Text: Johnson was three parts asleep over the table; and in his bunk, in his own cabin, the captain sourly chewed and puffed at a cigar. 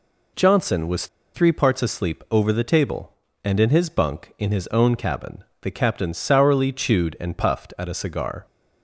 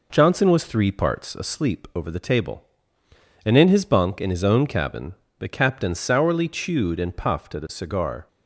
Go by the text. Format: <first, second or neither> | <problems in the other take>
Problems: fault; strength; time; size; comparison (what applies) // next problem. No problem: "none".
second | pauses between "was" and "three"; slight; at 1.0 s; 0.28 s long